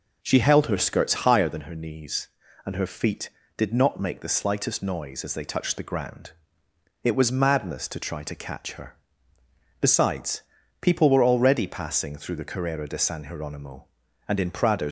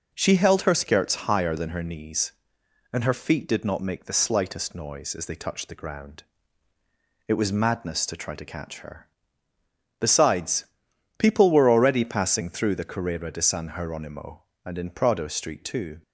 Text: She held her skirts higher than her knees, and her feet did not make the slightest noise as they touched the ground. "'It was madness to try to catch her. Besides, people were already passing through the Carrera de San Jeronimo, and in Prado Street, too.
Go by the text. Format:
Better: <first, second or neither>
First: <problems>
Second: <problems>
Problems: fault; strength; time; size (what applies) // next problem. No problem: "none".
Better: second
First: stops before "Street too"; at 14.8 s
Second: none